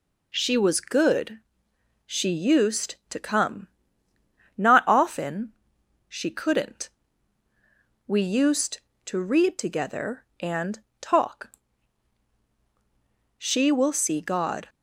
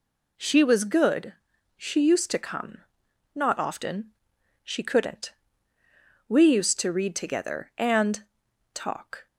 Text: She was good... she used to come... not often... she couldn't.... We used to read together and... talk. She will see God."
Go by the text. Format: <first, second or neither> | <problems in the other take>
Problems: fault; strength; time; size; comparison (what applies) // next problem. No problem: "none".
first | stops before "She will see God"; at 9.2 s